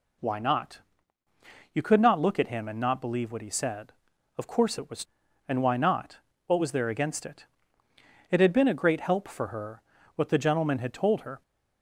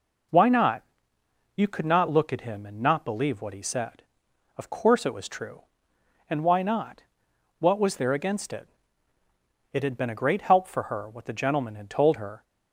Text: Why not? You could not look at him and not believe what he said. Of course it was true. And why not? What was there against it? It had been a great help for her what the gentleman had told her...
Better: second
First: skips "true"; at 5.2 s // pauses between "her" and "what"; slight; at 9.8 s; 0.34 s long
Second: none

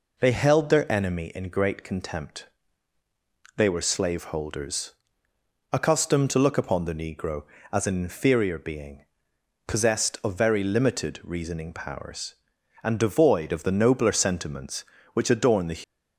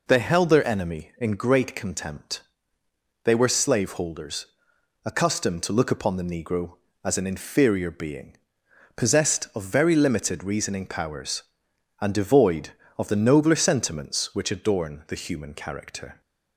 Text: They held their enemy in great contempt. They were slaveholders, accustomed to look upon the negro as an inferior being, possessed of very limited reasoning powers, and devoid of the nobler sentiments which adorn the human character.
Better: second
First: stops before "human character"; at 15.8 s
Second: none

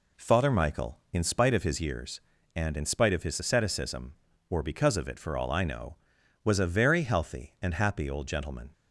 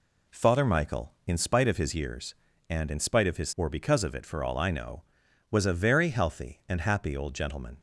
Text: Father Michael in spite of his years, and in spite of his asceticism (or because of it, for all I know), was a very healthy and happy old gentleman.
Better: first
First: none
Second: skips "asceticism"; at 3.5 s

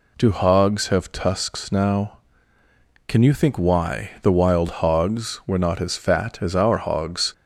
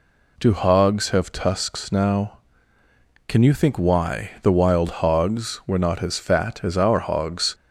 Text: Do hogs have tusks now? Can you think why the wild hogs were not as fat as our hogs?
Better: neither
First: none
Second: none

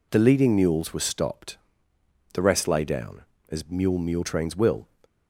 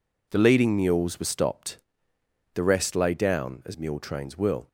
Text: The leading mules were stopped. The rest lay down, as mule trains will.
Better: second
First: says "mule" twice; at 3.9 s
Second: none

